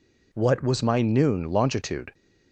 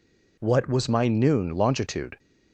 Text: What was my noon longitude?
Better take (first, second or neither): neither